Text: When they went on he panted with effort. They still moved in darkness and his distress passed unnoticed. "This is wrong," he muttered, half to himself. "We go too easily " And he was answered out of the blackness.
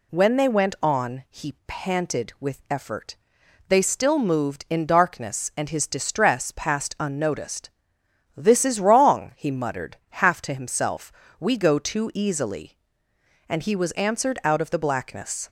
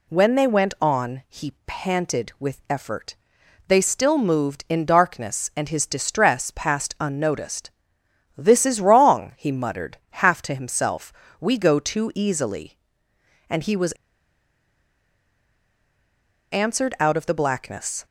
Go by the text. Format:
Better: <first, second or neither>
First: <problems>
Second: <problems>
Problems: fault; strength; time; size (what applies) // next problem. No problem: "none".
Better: first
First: none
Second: pauses between "was" and "answered"; strong; at 13.9 s; 2.6 s long